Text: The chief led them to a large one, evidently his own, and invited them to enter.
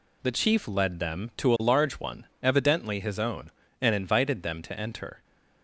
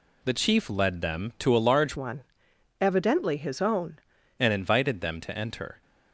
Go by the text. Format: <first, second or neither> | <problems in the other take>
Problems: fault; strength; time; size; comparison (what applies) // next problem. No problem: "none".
first | changes voice from "one" to "own"; from 1.9 to 3.9 s; 2.0 s long